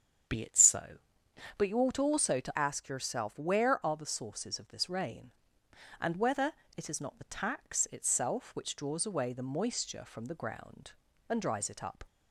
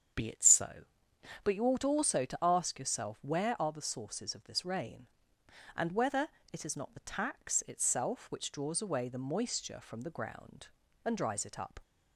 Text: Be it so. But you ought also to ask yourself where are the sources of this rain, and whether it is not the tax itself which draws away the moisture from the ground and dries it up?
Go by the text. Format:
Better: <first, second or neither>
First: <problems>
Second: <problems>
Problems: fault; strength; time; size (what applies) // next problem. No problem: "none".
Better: second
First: starts louder than the rest; strong; until 1.8 s; 7.5 dB // changes voice from "ask" to "where"; from 2.5 to 3.8 s; 1.3 s long // pauses between "whether" and "it"; slight; at 6.5 s; 0.24 s long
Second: starts louder than the rest; strong; until 1.7 s; 7.5 dB // pauses between "whether" and "it"; slight; at 6.2 s; 0.24 s long